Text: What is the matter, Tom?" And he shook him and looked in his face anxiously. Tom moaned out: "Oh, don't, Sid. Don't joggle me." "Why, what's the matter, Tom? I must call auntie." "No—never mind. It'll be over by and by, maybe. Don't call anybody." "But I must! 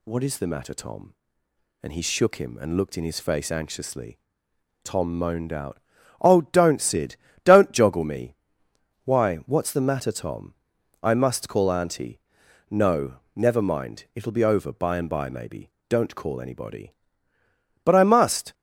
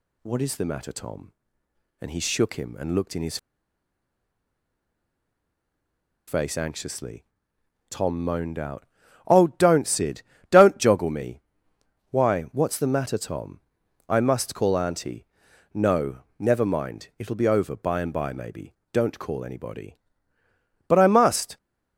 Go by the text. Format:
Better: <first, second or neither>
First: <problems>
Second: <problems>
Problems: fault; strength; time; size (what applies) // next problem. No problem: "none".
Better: first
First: none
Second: pauses between "his" and "face"; strong; at 3.3 s; 2.9 s long